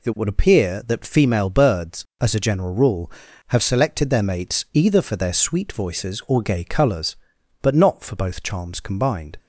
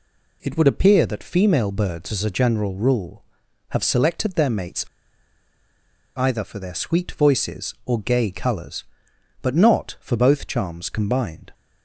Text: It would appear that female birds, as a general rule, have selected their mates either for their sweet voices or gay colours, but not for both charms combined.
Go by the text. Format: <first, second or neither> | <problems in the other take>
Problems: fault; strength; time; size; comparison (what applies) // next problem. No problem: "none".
first | pauses between "mates" and "either"; strong; at 4.8 s; 1.3 s long